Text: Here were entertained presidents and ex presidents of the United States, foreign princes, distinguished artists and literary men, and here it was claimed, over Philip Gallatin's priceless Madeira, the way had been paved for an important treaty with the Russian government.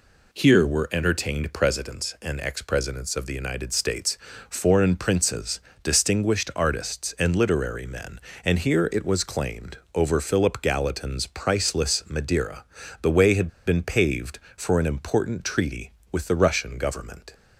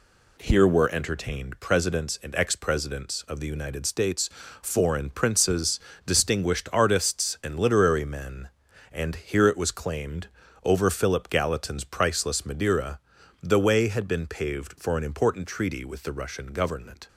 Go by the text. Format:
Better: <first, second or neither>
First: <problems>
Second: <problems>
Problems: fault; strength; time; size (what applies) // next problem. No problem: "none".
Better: second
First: pauses between "had" and "been"; slight; at 13.4 s; 0.16 s long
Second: none